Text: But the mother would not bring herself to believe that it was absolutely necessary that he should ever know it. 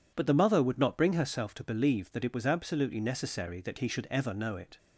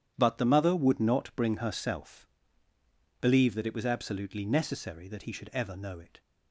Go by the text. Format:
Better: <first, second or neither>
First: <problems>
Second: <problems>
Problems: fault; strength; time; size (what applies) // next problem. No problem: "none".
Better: first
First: none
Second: starts louder than the rest; strong; until 1.1 s; 9.5 dB // skips "to"; at 2.7 s